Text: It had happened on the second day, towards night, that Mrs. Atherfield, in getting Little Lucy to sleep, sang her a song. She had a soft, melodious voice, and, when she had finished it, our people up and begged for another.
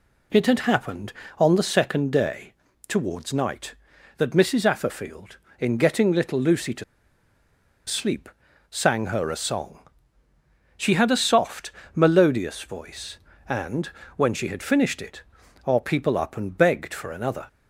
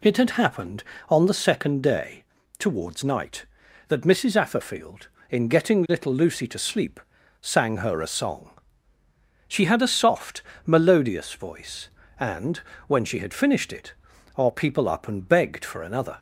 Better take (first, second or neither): second